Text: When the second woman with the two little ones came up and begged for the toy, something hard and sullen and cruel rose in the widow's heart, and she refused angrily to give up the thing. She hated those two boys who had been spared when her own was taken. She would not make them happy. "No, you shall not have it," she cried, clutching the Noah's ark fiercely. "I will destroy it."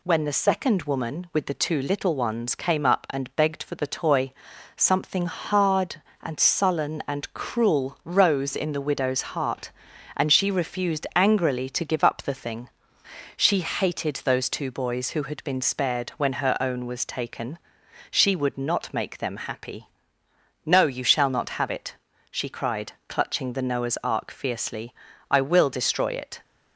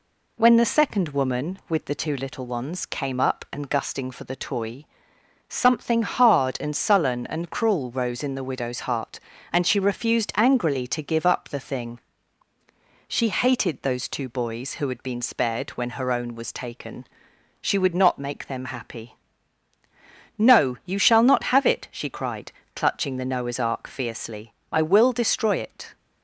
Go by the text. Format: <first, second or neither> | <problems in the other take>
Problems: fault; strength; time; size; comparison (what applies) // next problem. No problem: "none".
first | says "gusting" for "begged"; at 3.6 s